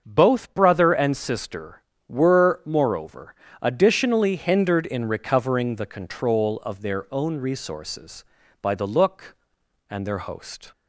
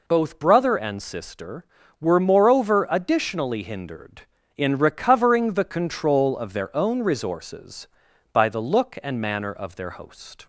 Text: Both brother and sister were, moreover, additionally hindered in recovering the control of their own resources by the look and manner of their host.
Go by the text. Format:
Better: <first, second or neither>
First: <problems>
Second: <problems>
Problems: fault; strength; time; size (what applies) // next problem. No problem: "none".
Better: second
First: starts louder than the rest; until 1.0 s; 6.5 dB // skips "manner of"; at 10.0 s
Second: none